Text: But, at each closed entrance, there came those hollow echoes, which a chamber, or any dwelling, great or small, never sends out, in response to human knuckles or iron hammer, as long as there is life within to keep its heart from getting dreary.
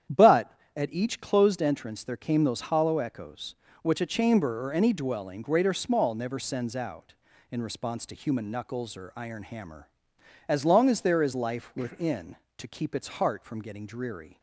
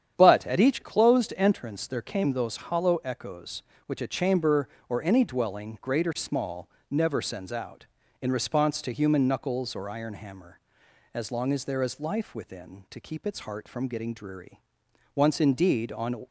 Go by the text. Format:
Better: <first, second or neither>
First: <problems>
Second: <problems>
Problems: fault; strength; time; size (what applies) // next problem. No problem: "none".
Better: first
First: starts louder than the rest; strong; until 1.3 s; 9.5 dB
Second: starts louder than the rest; strong; until 1.1 s; 9 dB // goes on to say "Once indeed on"; noticeable; from 15.1 s on; 1.1 s long